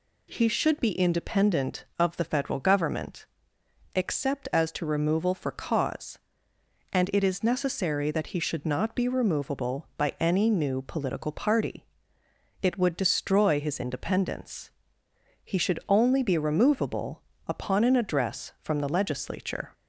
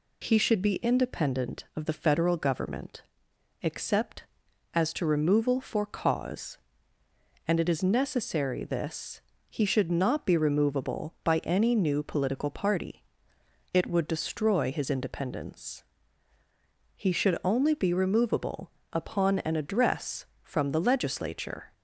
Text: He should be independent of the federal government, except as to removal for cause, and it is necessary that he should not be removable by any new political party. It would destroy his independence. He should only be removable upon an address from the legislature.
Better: first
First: pauses between "removable" and "upon"; slight; at 17.2 s; 0.24 s long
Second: says "this" for "that"; at 8.6 s // pauses between "removable" and "upon"; slight; at 18.7 s; 0.22 s long

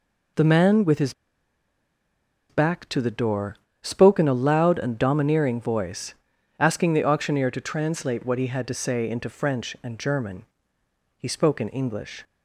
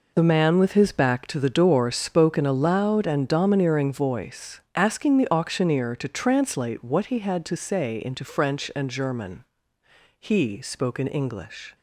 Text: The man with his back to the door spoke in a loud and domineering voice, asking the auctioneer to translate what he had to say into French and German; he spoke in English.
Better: second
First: pauses between "his" and "back"; strong; at 1.1 s; 1.3 s long // pauses between "door" and "spoke"; slight; at 3.5 s; 0.24 s long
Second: none

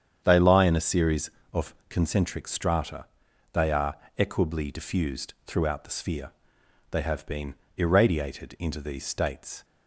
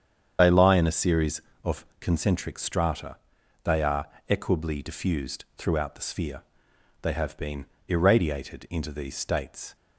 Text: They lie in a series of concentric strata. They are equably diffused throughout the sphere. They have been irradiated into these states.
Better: first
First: starts louder than the rest; strong; until 1.2 s; 8.5 dB // pauses between "are" and "equably"; slight; at 3.9 s; 0.22 s long // pauses between "been" and "irradiated"; slight; at 7.5 s; 0.22 s long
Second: loses the start of "They"; at 0.3 s; 40 ms // starts louder than the rest; strong; until 1.4 s; 8 dB // pauses between "are" and "equably"; slight; at 4.0 s; 0.22 s long // pauses between "been" and "irradiated"; slight; at 7.6 s; 0.22 s long

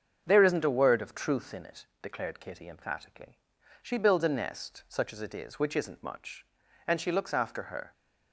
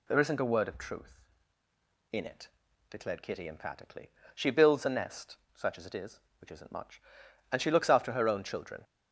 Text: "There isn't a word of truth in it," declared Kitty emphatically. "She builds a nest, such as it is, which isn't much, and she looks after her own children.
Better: second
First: starts louder than the rest; until 1.2 s; 7 dB // stops before "own children"; at 7.9 s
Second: none

